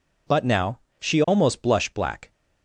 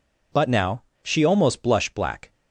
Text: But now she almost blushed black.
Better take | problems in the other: neither | pauses between "now" and "she"; slight; the same in both

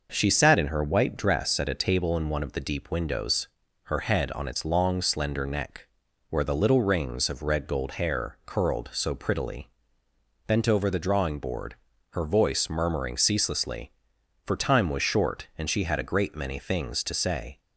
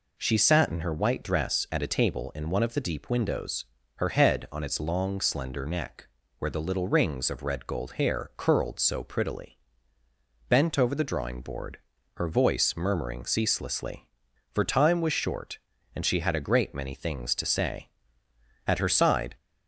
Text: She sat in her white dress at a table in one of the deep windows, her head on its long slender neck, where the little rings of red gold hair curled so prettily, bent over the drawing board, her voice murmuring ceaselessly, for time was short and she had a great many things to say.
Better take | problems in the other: first | goes on to say "At her side"; noticeable; from 18.6 s on; 0.70 s long

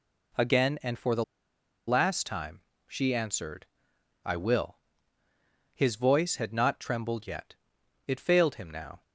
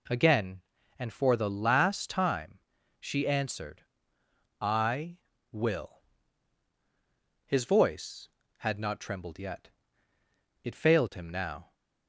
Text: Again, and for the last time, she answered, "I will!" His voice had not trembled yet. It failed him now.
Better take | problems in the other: second | pauses between "the" and "last"; noticeable; at 1.2 s; 0.63 s long

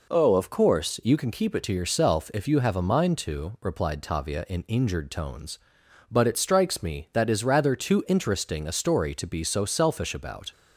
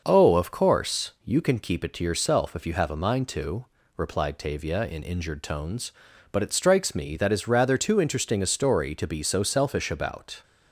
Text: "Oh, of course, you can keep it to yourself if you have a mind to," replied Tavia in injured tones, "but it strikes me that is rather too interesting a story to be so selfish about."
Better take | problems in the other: neither | none

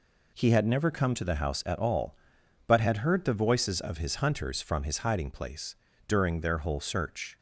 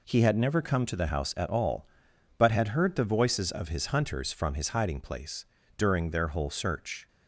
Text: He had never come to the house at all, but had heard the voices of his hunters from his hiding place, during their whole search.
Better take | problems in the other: neither | none

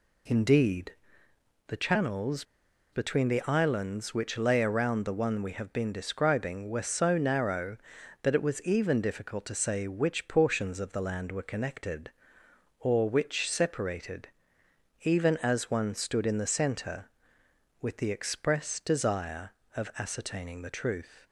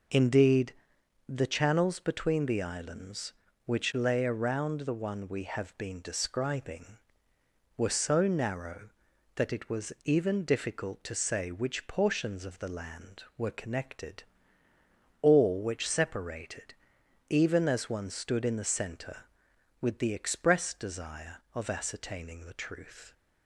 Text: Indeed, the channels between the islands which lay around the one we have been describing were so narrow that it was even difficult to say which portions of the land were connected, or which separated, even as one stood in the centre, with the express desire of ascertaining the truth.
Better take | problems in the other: second | pauses between "channels" and "between"; noticeable; at 2.4 s; 0.50 s long

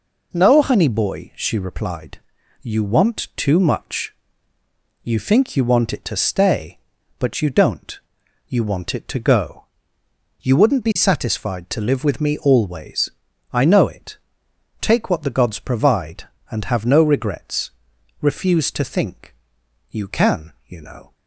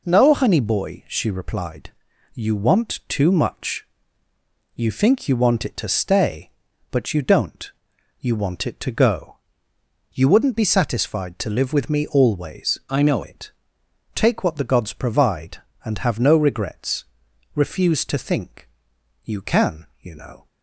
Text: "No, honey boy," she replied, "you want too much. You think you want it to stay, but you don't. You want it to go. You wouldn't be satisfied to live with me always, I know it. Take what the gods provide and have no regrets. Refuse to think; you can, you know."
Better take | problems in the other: first | changes voice from "I" to "know"; from 12.8 to 13.2 s; 0.4 s long

